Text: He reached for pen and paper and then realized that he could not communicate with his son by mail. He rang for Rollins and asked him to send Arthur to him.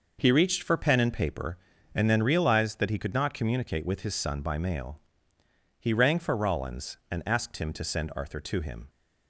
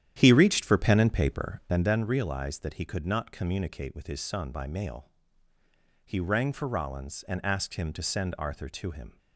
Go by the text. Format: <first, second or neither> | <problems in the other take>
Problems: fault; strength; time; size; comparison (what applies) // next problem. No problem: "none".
first | starts louder than the rest; strong; until 1.9 s; 10.5 dB